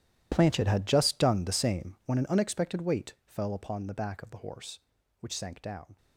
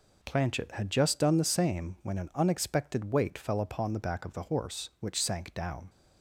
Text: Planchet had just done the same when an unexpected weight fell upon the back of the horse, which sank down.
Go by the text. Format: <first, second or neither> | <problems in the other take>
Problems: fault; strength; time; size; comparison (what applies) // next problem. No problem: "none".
second | gets quieter; strong; throughout; 18.5 dB